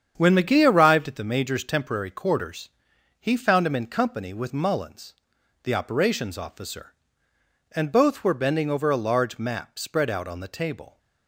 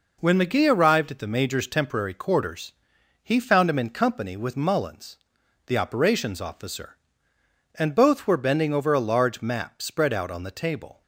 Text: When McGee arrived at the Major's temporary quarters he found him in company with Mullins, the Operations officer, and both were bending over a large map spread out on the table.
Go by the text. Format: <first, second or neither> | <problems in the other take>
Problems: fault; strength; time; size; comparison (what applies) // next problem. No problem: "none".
second | starts louder than the rest; strong; until 1.3 s; 8 dB // pauses between "quarters" and "he"; noticeable; at 2.7 s; 0.50 s long; noticeable in the second